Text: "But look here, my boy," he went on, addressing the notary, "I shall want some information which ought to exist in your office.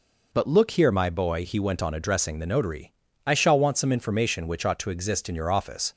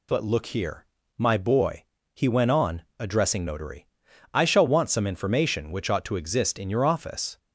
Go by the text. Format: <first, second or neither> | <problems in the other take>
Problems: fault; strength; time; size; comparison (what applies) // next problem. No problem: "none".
first | skips "the"; at 3.4 s